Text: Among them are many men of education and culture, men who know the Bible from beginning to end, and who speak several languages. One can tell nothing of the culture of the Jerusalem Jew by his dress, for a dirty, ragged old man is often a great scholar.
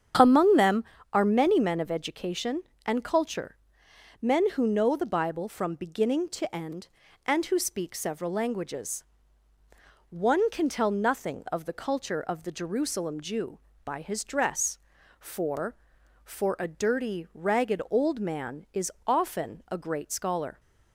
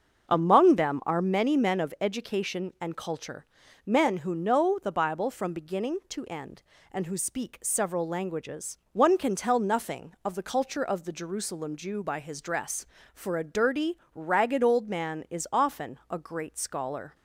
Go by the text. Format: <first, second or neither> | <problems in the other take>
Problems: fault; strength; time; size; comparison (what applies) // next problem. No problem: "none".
second | starts louder than the rest; strong; until 1.4 s; 8.5 dB; also in the second // says "for" twice; at 16.2 s // pauses between "is" and "often"; slight; at 18.8 s; 0.16 s long